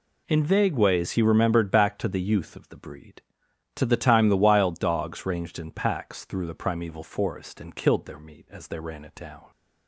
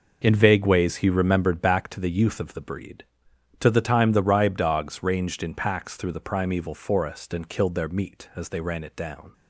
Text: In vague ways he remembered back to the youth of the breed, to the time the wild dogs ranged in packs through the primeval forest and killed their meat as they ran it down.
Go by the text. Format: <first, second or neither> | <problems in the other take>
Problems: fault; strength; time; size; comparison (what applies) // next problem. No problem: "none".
first | says "ribe" for "wild"; at 4.2 s